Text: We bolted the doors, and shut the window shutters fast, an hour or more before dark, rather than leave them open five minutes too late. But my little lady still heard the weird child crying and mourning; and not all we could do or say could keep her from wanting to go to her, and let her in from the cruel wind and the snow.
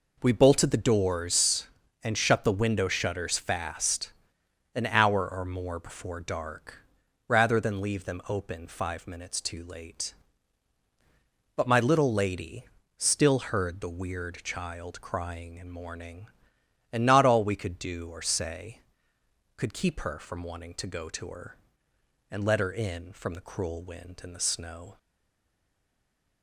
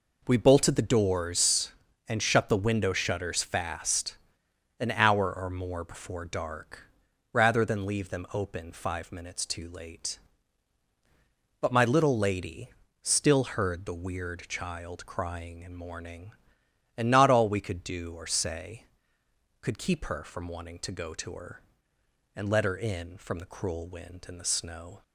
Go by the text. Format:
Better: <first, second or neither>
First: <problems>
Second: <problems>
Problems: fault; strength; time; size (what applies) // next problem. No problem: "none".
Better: second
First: pauses between "lady" and "still"; slight; at 12.6 s; 0.34 s long // stays silent after the last word; noticeable; from 24.9 s on; 1.5 s long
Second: pauses between "lady" and "still"; slight; at 12.6 s; 0.34 s long